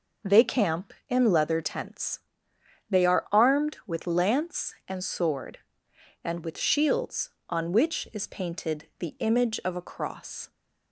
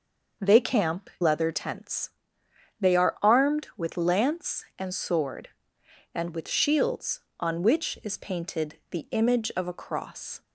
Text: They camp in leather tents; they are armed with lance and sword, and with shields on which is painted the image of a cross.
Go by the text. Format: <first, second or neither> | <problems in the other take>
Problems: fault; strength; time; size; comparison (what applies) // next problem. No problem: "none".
first | skips "in"; at 1.1 s